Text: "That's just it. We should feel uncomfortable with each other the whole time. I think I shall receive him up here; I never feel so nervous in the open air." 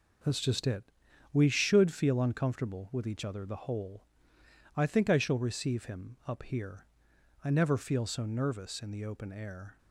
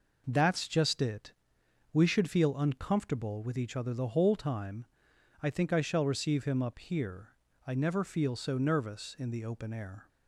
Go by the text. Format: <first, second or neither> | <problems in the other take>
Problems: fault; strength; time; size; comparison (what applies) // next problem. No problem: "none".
second | skips "time"; at 4.3 s